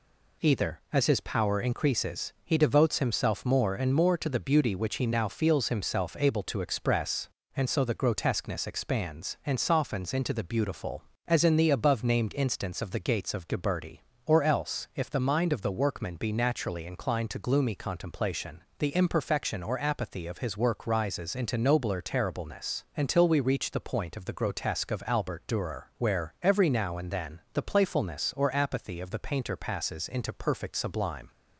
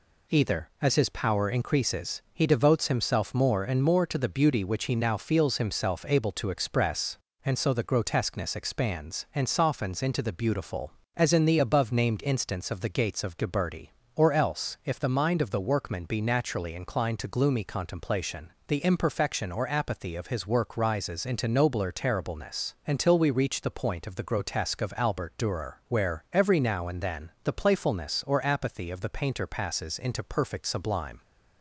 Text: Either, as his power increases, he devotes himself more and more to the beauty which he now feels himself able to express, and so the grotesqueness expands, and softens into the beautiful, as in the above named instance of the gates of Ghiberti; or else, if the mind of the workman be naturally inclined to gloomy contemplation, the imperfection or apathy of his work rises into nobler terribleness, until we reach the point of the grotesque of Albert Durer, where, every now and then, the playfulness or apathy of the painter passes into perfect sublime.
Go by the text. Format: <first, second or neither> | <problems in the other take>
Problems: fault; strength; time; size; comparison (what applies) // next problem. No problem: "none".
neither | none